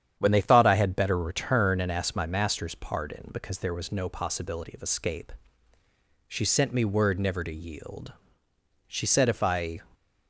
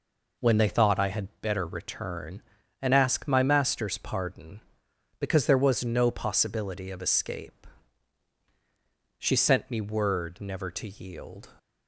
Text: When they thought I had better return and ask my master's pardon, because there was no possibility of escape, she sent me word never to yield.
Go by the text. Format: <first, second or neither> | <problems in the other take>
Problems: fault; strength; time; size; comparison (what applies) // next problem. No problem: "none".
second | starts louder than the rest; strong; until 1.2 s; 9 dB // goes on to say "She said if I"; noticeable; from 8.8 s on; 0.92 s long